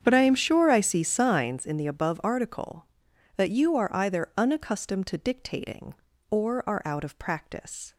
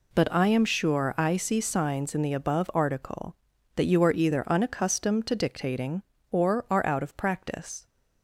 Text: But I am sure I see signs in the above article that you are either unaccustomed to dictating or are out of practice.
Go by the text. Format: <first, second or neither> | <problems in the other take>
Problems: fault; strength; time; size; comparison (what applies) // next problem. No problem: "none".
second | starts louder than the rest; strong; until 1.6 s; 8 dB